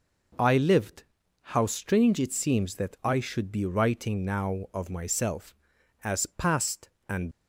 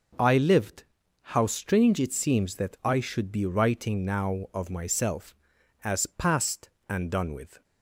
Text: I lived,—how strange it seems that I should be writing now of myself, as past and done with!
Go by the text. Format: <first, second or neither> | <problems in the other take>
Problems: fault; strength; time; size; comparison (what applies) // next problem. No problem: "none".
second | stops before "done with"; at 7.3 s